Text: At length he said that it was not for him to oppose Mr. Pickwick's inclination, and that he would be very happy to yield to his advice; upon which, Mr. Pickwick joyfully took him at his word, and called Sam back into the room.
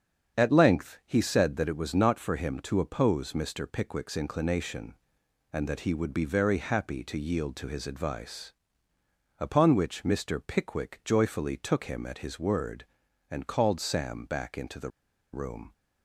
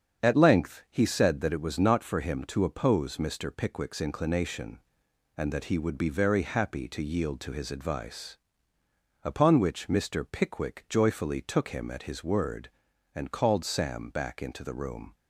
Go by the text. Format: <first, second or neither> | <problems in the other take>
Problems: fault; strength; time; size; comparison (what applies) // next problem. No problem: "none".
second | starts louder than the rest; strong; until 1.4 s; 7.5 dB; strong in the second // pauses between "the" and "room"; at 14.8 s; 0.42 s long